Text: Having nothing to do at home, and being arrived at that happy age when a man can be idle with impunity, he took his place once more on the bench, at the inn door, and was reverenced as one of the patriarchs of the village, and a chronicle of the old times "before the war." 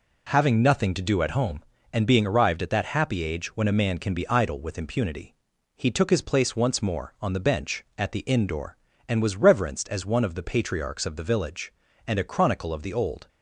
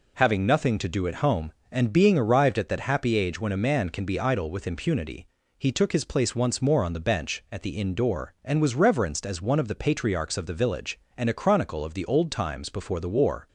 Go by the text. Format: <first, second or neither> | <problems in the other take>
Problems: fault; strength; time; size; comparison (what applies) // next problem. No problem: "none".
second | stops before "times before the war"; at 13.2 s